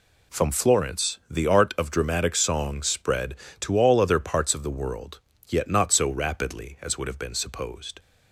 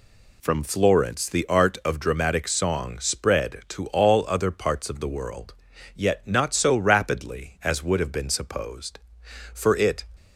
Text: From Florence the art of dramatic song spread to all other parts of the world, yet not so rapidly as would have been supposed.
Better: first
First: none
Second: goes on to say "For it"; from 9.5 s on; 0.52 s long

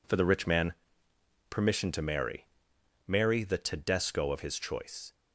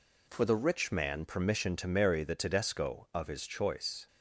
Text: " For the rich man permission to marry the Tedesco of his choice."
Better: second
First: pauses between "man" and "permission"; noticeable; at 0.7 s; 0.74 s long // says "marry" twice; at 3.0 s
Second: none

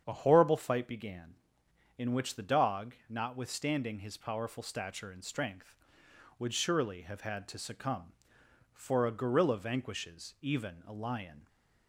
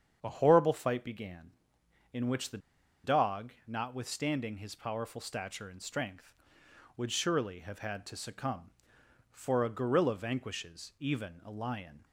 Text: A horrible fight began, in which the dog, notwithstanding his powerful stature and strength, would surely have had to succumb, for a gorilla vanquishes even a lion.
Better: first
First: starts louder than the rest; strong; until 1.0 s; 8 dB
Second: starts louder than the rest; strong; until 1.2 s; 8 dB // pauses between "the" and "dog"; at 2.5 s; 0.45 s long

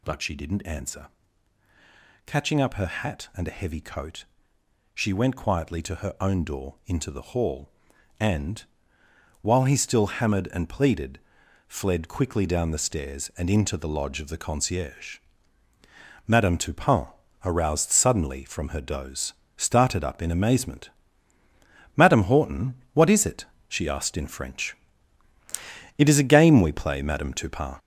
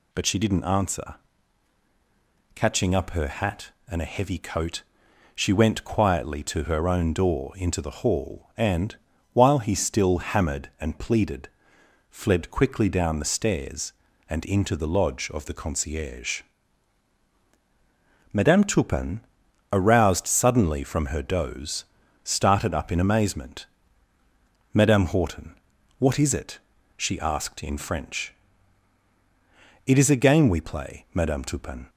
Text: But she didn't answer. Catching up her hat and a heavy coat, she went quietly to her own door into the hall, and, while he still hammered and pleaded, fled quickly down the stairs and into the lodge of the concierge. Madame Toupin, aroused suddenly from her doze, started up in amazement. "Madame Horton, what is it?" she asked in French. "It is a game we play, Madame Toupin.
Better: second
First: gets louder; noticeable; throughout; 5.5 dB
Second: none

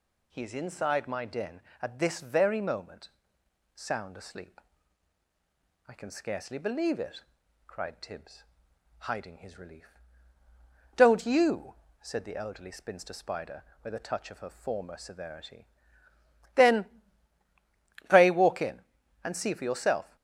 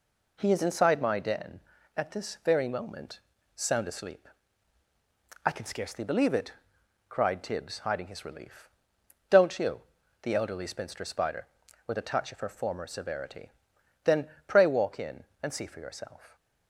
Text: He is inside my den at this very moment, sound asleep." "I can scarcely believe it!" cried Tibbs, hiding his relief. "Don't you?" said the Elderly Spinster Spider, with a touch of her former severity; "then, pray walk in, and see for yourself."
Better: first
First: none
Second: skips "said"; at 10.0 s

